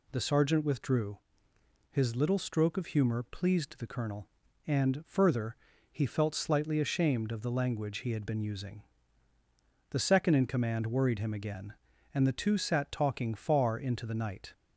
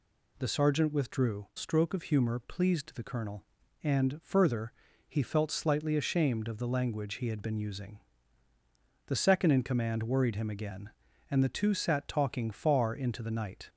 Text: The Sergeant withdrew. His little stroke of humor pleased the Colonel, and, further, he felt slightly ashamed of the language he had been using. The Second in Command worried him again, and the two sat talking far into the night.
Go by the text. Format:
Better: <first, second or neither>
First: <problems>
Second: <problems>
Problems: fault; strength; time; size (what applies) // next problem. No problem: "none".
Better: first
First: none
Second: skips "His little"; at 1.5 s